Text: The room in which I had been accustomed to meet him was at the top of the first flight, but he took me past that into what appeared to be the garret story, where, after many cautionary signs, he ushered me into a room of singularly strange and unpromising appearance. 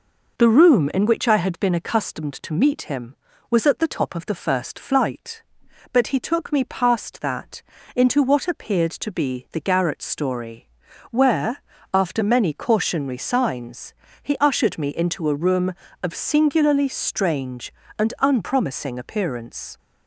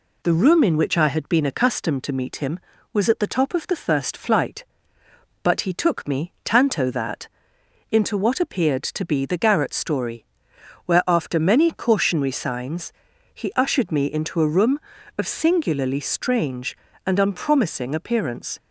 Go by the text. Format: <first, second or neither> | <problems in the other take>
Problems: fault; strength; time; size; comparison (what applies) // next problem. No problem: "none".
first | says "tanto" for "past"; at 6.4 s // pauses between "that" and "into"; noticeable; at 7.2 s; 0.64 s long; slight in the first